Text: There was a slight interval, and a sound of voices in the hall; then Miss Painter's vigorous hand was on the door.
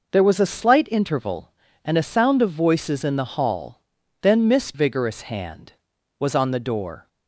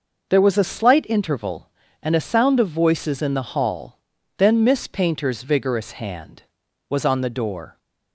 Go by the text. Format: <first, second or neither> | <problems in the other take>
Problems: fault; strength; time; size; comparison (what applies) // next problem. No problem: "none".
second | skips "Painter's"; at 4.7 s